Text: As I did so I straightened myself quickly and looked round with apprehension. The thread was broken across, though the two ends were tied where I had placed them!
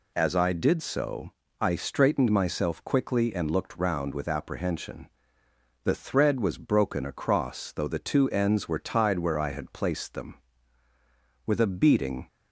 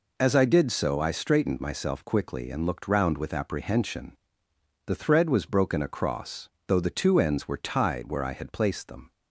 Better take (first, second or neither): second